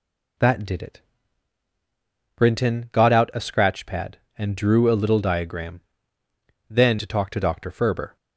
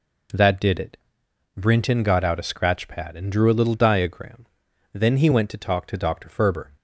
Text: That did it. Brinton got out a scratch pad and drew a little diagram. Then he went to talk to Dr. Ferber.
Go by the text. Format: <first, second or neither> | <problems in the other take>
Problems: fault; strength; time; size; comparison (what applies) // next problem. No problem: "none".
second | skips "he went"; at 6.9 s